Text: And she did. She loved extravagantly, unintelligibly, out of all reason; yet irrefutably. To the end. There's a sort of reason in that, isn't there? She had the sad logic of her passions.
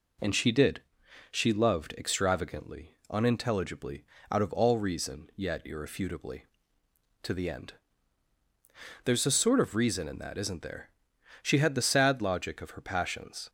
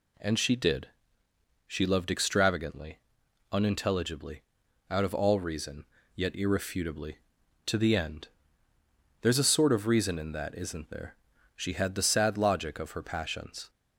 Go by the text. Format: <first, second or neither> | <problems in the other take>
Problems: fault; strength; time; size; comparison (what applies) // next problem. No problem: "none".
neither | none